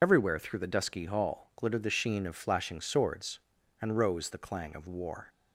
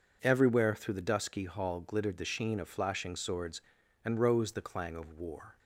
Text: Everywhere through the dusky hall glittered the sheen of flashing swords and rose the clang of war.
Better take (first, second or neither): second